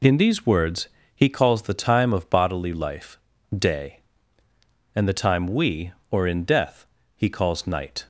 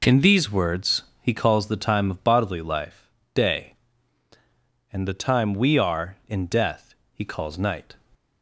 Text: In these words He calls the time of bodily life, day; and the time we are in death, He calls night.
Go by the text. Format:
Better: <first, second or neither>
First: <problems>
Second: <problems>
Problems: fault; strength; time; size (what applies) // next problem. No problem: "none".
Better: second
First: pauses between "words" and "He"; slight; at 0.8 s; 0.26 s long // says "or" for "are"; at 6.1 s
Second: pauses between "words" and "He"; slight; at 1.0 s; 0.18 s long